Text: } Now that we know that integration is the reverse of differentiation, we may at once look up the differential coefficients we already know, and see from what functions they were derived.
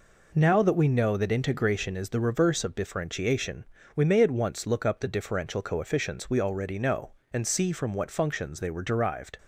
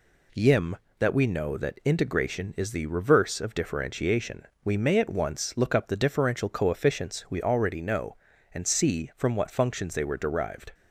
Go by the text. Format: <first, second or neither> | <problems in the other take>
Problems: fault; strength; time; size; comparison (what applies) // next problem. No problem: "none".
first | says "Yim" for "Now"; at 0.3 s